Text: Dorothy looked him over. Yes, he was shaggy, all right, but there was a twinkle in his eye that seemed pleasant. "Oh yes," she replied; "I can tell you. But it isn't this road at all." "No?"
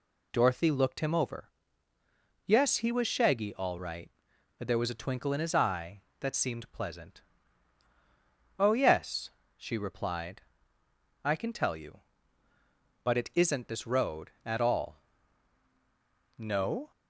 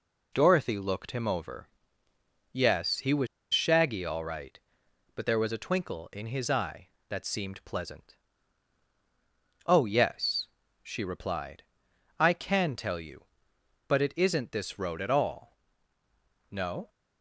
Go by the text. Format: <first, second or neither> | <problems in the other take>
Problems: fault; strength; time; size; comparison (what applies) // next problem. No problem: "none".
first | pauses between "was" and "shaggy"; slight; at 3.2 s; 0.25 s long